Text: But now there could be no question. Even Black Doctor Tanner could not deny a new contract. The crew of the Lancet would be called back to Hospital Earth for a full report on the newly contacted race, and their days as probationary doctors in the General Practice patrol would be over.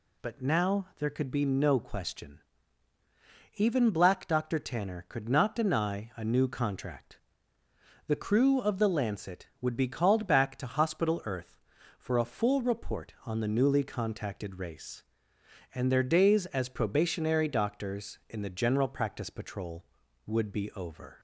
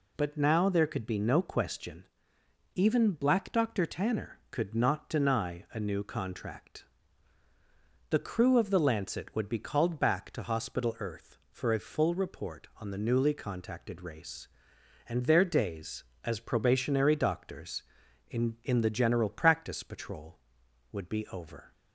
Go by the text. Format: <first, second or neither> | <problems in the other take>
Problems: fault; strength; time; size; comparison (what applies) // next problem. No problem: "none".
first | says "in" twice; at 18.6 s